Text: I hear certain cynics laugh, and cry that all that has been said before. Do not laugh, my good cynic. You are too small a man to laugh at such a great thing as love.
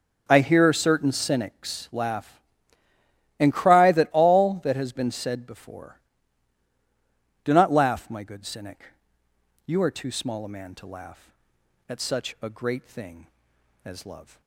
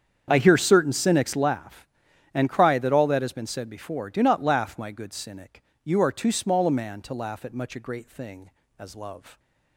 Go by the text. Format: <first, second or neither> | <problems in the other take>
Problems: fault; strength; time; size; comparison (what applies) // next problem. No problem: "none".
first | starts louder than the rest; strong; until 1.3 s; 8 dB; also in the first // says "much" for "such"; at 7.5 s